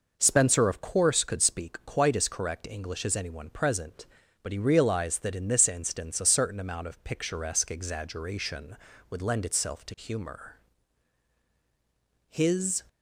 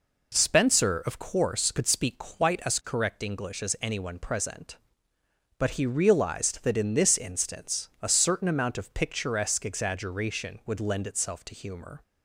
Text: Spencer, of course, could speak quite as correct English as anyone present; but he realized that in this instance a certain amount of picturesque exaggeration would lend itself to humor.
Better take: second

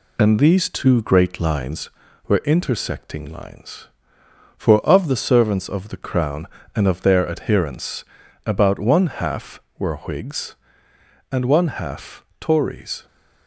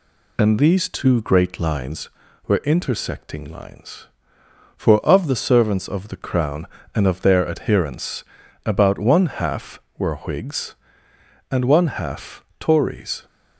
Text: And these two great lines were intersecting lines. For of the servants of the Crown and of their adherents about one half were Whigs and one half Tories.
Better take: second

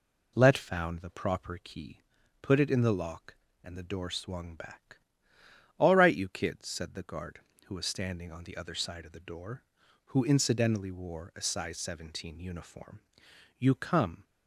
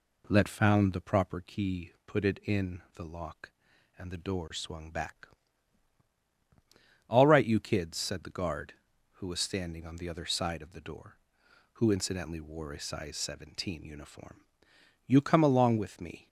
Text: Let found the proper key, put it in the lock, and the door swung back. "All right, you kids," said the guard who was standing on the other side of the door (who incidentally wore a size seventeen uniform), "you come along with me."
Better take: second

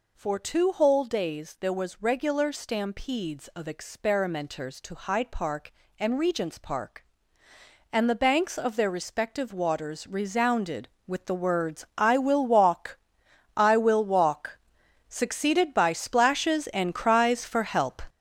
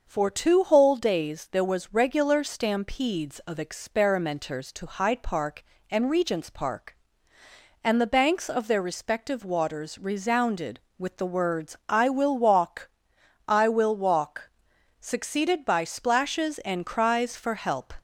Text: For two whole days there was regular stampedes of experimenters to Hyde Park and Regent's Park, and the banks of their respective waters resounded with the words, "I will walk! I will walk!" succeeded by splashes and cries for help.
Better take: second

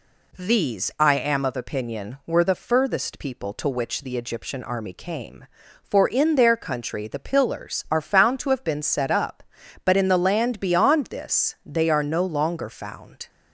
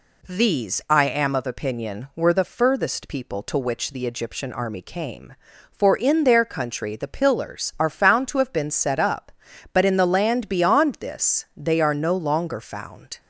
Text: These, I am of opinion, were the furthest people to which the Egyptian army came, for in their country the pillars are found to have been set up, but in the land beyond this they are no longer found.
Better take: neither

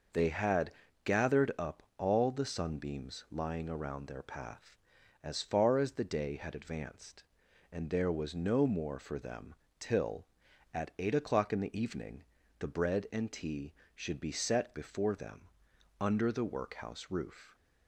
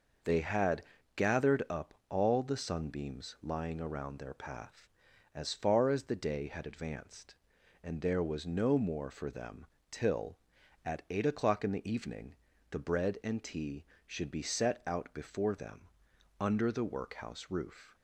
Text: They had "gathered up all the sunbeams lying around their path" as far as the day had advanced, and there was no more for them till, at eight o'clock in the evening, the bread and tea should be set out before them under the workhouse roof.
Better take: second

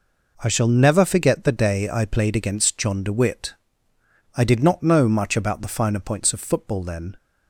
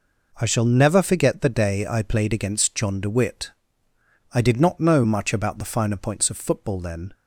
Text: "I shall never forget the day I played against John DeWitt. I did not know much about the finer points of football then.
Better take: neither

